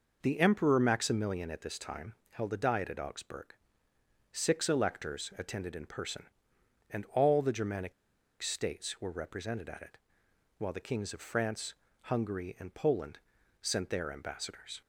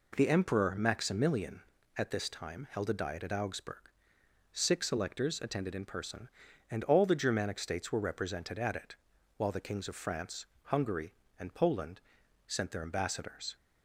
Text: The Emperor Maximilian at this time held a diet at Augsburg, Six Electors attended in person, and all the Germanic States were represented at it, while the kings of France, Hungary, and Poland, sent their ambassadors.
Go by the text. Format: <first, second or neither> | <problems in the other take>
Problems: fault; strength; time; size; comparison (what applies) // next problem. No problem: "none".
second | pauses between "time" and "held"; slight; at 2.1 s; 0.16 s long // pauses between "Germanic" and "States"; noticeable; at 7.9 s; 0.48 s long